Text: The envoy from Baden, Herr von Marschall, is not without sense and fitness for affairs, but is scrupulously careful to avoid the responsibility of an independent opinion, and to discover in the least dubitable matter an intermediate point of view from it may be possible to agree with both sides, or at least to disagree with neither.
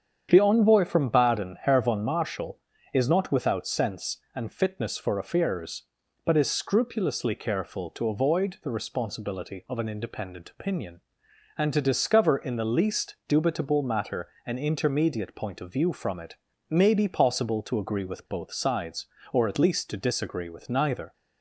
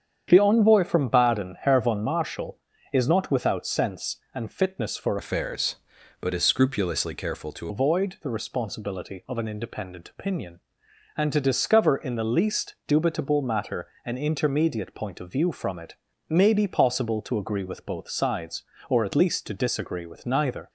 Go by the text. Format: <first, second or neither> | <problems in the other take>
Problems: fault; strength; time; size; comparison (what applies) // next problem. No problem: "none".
first | starts louder than the rest; strong; until 1.2 s; 8 dB; strong in the first // changes voice from "affairs" to "to"; from 5.1 to 7.6 s; 2.5 s long // pauses between "matter" and "an"; slight; at 13.8 s; 0.18 s long; slight in the first // pauses between "it" and "may"; slight; at 15.9 s; 0.34 s long; slight in the first